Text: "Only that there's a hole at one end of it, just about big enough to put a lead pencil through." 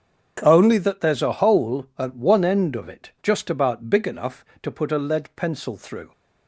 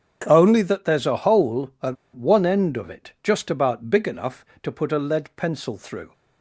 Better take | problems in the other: first | starts louder than the rest; strong; until 1.2 s; 8.5 dB; strong in the first // pauses between "at" and "one"; slight; at 1.9 s; 0.19 s long

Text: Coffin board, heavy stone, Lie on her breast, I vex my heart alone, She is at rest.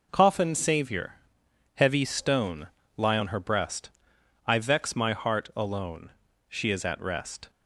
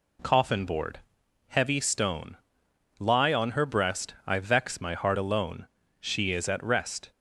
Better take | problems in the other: second | says "savior" for "board"; at 0.5 s

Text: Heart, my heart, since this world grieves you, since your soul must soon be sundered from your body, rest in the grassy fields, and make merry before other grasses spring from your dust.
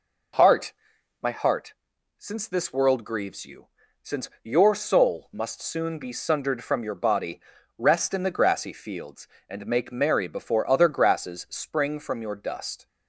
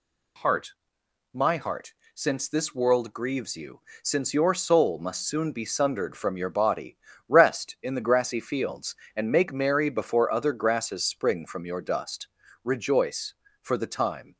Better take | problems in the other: first | goes on to say "Rejoice for the time"; strong; from 12.6 s on; 1.7 s long

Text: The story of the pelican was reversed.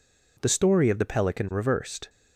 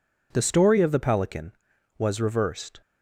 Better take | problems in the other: second | skips "was"; at 1.5 s

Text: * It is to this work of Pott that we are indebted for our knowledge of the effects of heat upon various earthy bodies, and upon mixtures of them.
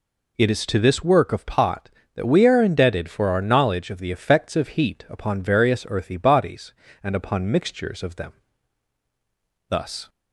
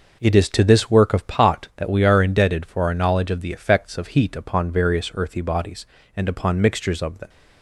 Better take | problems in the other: second | goes on to say "Thus"; slight; from 9.6 s on; 0.40 s long

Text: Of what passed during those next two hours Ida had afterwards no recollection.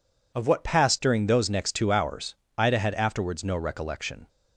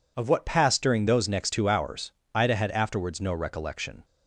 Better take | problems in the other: neither | pauses between "hours" and "Ida"; slight; the same in both

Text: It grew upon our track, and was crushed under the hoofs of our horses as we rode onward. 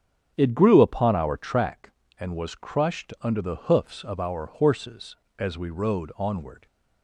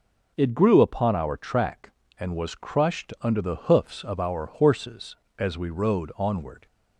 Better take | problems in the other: second | starts louder than the rest; strong; until 1.7 s; 7.5 dB

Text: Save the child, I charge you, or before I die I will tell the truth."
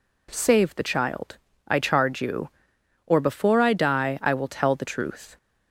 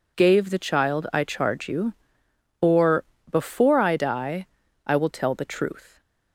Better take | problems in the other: first | says "Gave" for "Save"; at 0.1 s // pauses between "or" and "before"; slight; at 3.0 s; 0.26 s long // pauses between "die" and "I"; at 4.4 s; 0.38 s long

